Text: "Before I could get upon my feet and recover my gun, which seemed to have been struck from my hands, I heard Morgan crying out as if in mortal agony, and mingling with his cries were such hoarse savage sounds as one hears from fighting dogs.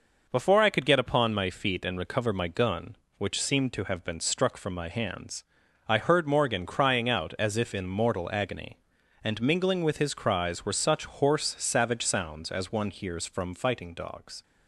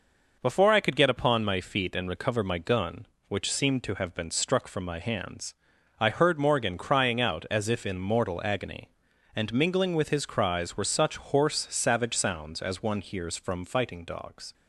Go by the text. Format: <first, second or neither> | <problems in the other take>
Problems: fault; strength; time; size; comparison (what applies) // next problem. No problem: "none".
neither | none